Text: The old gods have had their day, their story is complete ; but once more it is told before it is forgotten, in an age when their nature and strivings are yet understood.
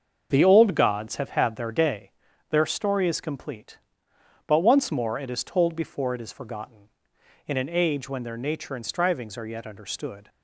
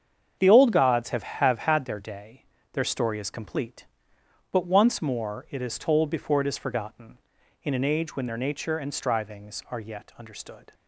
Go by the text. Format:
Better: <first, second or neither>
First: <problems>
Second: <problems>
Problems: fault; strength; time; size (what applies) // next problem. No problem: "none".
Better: first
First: starts louder than the rest; until 1.3 s; 6.5 dB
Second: starts louder than the rest; strong; until 1.4 s; 7.5 dB // says "have" twice; at 1.2 s